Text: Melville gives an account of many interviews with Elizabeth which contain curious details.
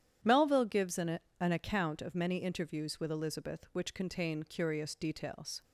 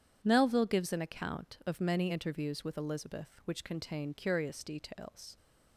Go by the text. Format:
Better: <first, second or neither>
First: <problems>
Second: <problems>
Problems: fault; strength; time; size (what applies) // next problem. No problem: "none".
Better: second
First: starts louder than the rest; strong; until 1.4 s; 10 dB // says "an" twice; at 1.3 s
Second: none